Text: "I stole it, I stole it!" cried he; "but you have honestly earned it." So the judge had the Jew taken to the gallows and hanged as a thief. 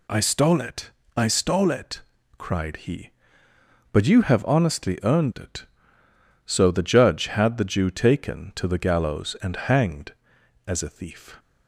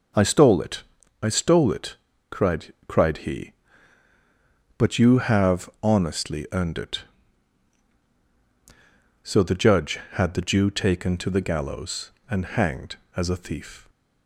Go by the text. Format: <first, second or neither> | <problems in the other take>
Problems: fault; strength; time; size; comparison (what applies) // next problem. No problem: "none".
first | says "cried" twice; at 2.8 s